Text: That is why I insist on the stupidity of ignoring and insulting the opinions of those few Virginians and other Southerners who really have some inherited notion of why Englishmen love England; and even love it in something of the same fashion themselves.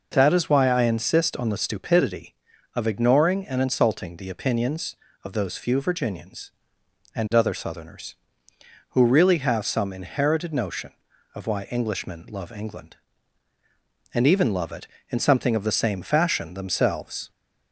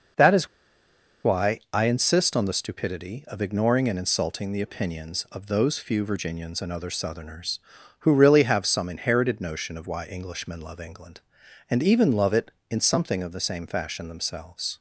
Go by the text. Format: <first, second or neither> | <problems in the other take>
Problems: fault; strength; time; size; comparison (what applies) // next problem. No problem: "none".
first | pauses between "is" and "why"; noticeable; at 0.4 s; 0.77 s long